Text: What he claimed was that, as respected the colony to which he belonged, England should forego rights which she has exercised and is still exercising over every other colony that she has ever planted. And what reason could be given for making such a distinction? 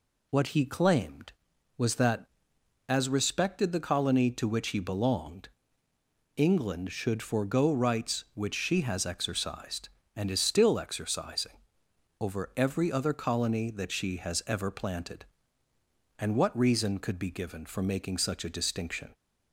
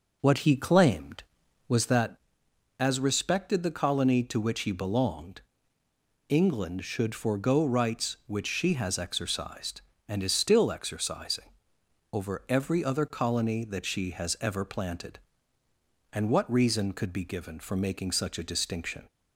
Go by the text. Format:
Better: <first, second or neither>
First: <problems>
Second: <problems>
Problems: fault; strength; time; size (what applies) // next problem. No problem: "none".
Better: first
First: pauses between "exercising" and "over"; noticeable; at 11.5 s; 0.62 s long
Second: starts louder than the rest; noticeable; until 2.0 s; 5 dB // pauses between "exercising" and "over"; noticeable; at 11.4 s; 0.62 s long